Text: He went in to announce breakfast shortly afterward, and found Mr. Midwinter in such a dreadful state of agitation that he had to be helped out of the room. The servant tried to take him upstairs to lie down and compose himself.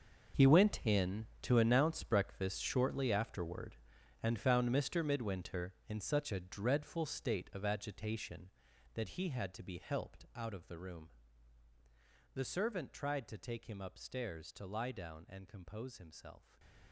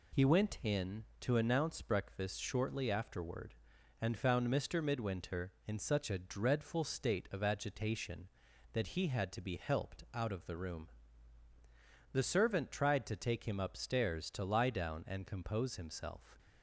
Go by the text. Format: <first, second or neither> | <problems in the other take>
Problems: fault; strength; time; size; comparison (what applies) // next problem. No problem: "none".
second | gets quieter; strong; throughout; 14 dB